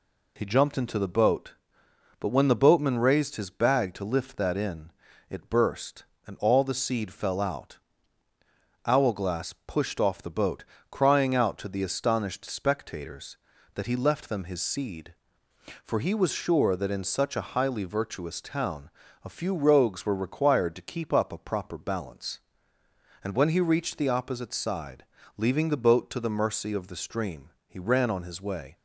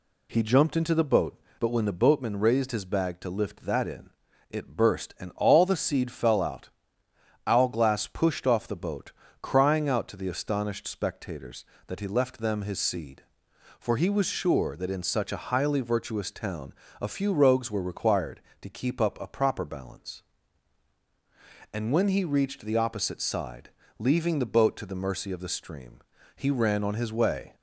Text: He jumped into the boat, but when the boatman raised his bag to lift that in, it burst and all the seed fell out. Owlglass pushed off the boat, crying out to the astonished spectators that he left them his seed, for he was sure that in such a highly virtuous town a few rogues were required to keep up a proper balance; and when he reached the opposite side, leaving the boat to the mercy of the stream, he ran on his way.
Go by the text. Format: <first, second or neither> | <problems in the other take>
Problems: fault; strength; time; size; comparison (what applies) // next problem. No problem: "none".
neither | pauses between "town" and "a"; slight; the same in both